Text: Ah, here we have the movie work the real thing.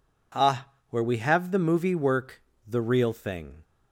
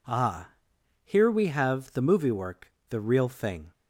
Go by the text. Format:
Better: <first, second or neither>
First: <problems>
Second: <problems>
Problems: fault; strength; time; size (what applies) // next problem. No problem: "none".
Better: second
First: says "where" for "here"; at 0.8 s // pauses between "work" and "the"; slight; at 2.4 s; 0.26 s long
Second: pauses between "work" and "the"; slight; at 2.7 s; 0.16 s long